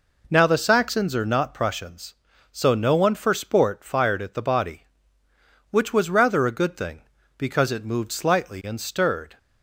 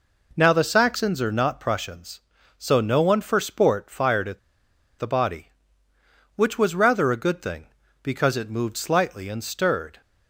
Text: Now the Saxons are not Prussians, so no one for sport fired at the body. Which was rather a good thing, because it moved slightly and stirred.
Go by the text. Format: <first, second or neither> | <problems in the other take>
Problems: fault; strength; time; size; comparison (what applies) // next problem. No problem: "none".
first | pauses between "at" and "the"; noticeable; at 4.3 s; 0.59 s long